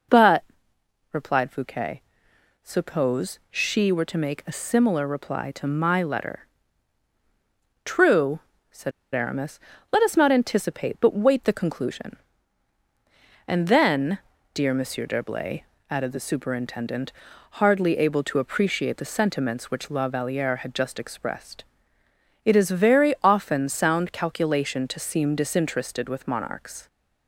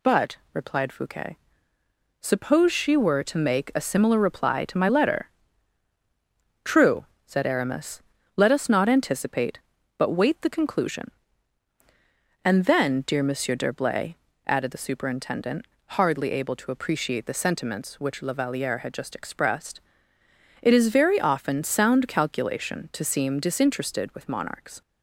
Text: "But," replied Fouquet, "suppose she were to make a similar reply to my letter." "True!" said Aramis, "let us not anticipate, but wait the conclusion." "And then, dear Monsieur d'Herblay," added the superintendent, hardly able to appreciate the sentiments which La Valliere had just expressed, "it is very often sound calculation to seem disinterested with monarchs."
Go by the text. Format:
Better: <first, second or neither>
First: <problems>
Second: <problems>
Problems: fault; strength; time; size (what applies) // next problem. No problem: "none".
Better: second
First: pauses between "said" and "Aramis"; slight; at 8.9 s; 0.21 s long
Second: none